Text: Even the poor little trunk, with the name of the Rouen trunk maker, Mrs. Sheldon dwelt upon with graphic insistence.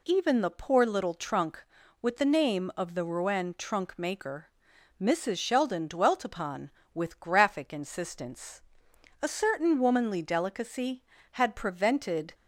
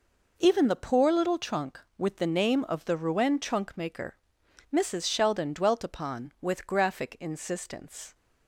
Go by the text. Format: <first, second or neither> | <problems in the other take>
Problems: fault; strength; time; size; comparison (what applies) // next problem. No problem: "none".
second | goes on to say "A certain womanly delicacy had prevented"; strong; from 9.2 s on; 3.1 s long